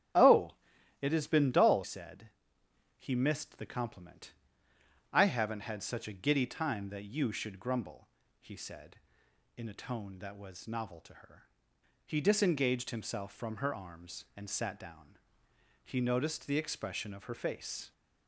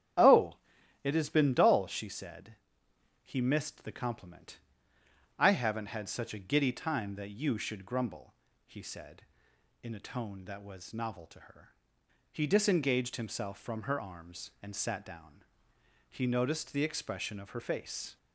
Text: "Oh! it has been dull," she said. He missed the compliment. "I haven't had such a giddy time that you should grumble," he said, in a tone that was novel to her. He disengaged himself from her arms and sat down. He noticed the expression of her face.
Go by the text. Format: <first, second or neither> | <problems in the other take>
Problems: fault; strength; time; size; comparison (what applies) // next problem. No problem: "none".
second | starts louder than the rest; strong; until 1.6 s; 9.5 dB; strong in the second // skips "she"; at 1.8 s